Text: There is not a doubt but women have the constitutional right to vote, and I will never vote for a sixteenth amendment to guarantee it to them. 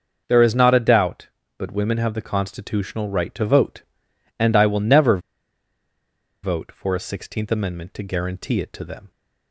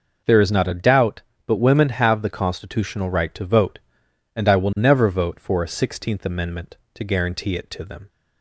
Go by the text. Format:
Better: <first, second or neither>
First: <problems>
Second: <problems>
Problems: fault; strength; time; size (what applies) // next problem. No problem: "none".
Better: second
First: starts louder than the rest; until 1.2 s; 6 dB // pauses between "never" and "vote"; strong; at 5.1 s; 1.2 s long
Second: none